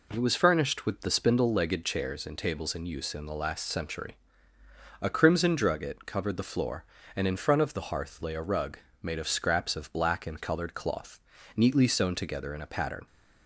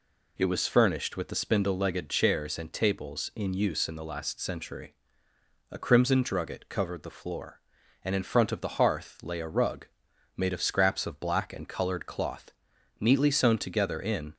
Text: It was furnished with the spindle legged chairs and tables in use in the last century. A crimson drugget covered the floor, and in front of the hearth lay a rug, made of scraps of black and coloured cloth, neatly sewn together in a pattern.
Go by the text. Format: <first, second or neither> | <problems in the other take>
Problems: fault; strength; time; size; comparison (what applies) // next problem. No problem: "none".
first | stops before "a pattern"; at 14.3 s